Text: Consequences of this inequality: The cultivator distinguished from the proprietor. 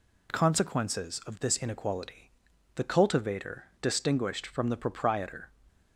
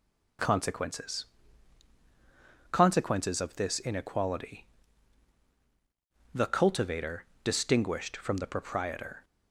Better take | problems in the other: first | says "Consequences" twice; at 2.7 s // pauses between "cultivator" and "distinguished"; slight; at 7.2 s; 0.18 s long; slight in the first

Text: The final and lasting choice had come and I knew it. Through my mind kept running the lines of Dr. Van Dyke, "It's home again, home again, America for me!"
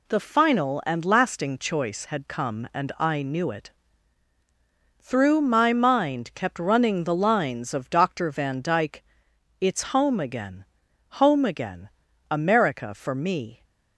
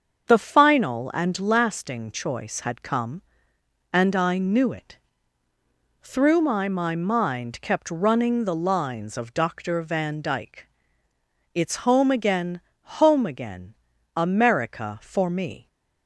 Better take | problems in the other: first | starts louder than the rest; until 1.3 s; 7 dB // says "my" twice; at 6.6 s

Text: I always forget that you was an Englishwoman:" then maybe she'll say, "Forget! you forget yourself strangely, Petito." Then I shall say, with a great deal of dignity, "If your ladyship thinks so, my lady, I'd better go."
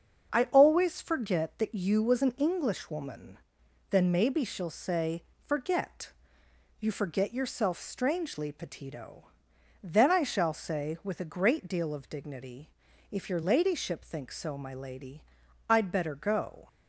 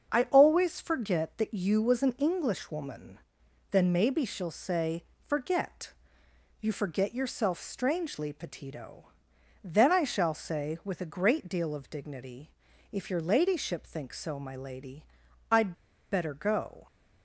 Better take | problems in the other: first | starts louder than the rest; until 1.1 s; 7 dB; also in the first // pauses between "I'd" and "better"; at 15.7 s; 0.38 s long

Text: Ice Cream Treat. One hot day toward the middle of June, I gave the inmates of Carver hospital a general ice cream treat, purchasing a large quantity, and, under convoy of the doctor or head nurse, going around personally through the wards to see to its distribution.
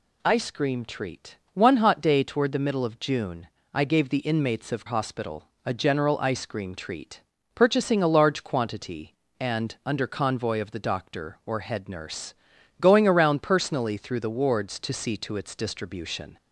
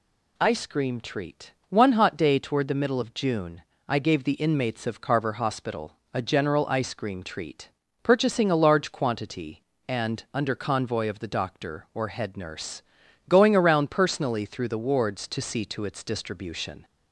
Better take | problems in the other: second | skips "Carver"; at 4.8 s // pauses between "hospital" and "a"; slight; at 5.4 s; 0.18 s long; slight in the second

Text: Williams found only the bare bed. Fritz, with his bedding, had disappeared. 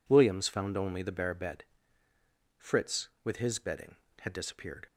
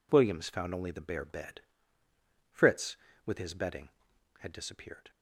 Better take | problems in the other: neither | none

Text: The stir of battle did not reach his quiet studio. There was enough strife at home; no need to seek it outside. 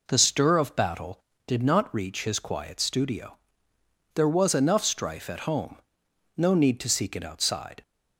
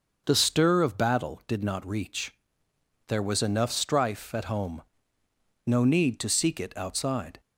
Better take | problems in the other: first | starts louder than the rest; until 1.2 s; 6.5 dB // skips "his quiet studio"; at 2.6 s

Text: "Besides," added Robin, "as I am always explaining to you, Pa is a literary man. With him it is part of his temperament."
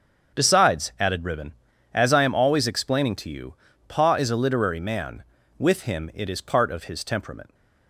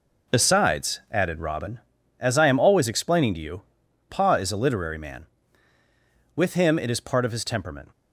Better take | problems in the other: second | starts louder than the rest; until 1.4 s; 7 dB // says "Ribbon" for "Robin"; at 1.2 s

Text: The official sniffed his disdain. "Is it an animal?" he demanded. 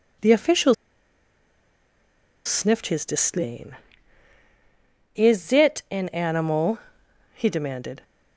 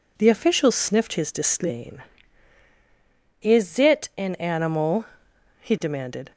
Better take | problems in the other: second | pauses between "official" and "sniffed"; strong; at 0.7 s; 1.7 s long

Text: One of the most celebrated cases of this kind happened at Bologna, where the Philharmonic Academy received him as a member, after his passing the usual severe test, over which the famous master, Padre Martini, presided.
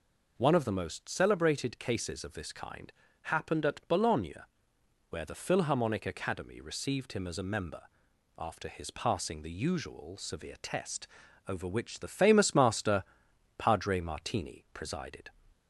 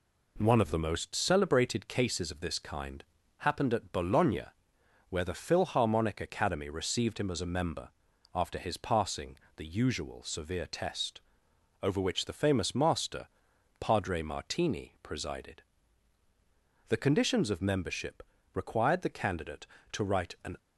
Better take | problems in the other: first | pauses between "kind" and "happened"; slight; at 3.0 s; 0.32 s long; slight in the first // pauses between "passing" and "the"; slight; at 9.3 s; 0.18 s long // goes on to say "The conditions of membership required the candidate to write an"; strong; from 16.8 s on; 3.6 s long

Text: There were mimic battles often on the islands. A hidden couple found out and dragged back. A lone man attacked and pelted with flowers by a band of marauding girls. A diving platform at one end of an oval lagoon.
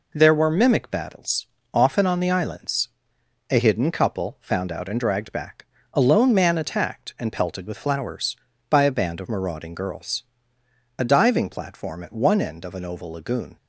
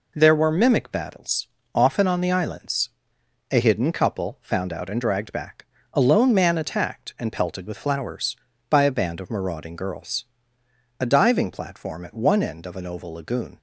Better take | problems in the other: neither | pauses between "battles" and "often"; slight; the same in both

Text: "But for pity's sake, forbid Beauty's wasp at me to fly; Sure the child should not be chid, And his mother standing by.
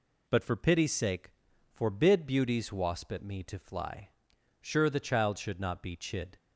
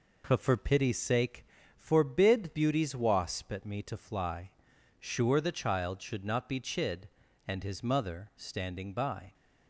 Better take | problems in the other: second | stops before "And his mother standing by"; at 6.3 s

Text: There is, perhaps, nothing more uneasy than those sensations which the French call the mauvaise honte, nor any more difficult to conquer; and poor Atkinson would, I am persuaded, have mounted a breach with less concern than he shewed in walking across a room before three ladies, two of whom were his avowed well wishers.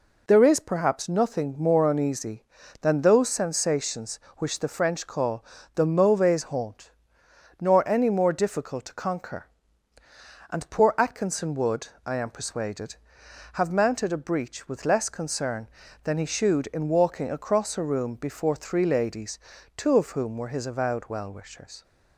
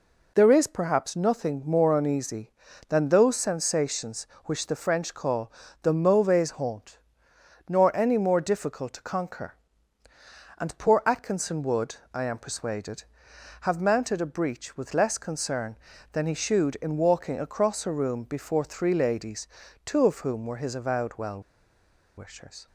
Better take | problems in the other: first | pauses between "call" and "the"; slight; at 5.5 s; 0.30 s long; slight in the first // pauses between "well" and "wishers"; noticeable; at 21.4 s; 0.75 s long

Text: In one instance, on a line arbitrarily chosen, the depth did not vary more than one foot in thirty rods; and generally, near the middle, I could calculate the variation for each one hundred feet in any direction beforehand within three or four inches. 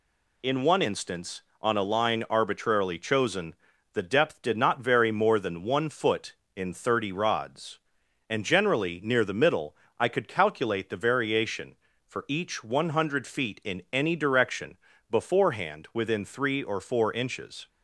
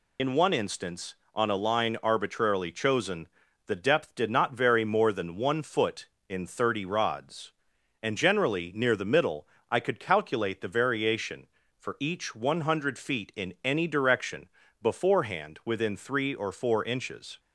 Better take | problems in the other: first | loses the start of "In"; at 0.1 s; 70 ms // pauses between "direction" and "beforehand"; slight; at 14.4 s; 0.34 s long; slight in the first

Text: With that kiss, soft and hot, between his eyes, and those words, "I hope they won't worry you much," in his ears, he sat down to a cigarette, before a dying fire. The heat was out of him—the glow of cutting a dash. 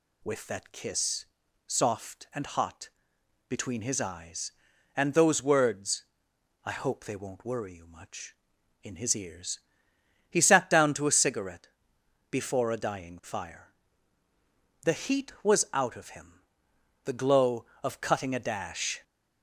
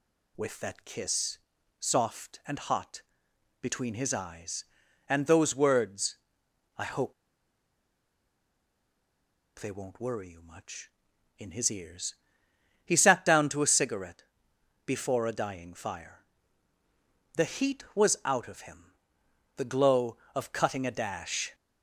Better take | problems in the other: first | pauses between "hope" and "they"; strong; at 7.1 s; 2.4 s long

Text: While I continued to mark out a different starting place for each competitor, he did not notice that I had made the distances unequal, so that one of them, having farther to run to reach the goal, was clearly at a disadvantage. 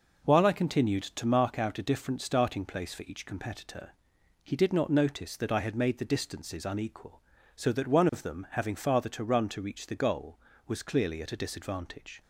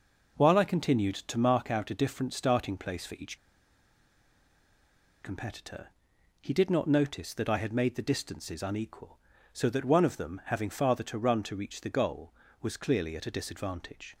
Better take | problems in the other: first | pauses between "each" and "competitor"; strong; at 3.3 s; 1.8 s long

